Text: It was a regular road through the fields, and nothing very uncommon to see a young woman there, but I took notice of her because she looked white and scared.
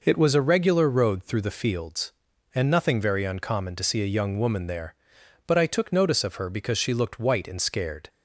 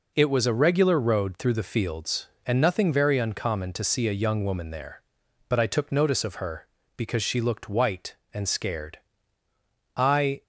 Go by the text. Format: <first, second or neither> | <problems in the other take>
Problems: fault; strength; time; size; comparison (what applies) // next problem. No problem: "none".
first | goes on to say "I"; slight; from 9.9 s on; 0.46 s long